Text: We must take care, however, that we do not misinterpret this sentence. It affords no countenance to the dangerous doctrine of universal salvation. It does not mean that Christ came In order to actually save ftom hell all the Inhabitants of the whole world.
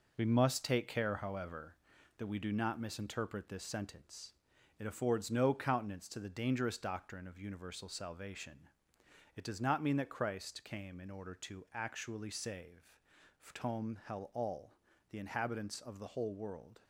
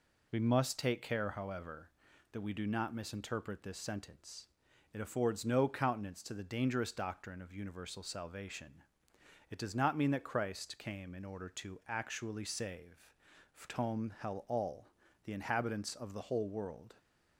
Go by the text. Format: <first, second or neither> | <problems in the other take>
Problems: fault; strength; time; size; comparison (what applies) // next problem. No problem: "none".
second | gets quieter; throughout; 7 dB // pauses between "save" and "ftom"; at 13.0 s; 0.44 s long; also in the second // pauses between "all" and "the"; slight; at 14.7 s; 0.36 s long; slight in the second